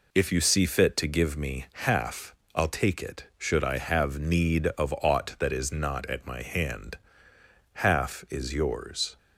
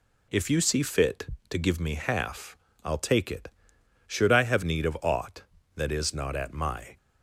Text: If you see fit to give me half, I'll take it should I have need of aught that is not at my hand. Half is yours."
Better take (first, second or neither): first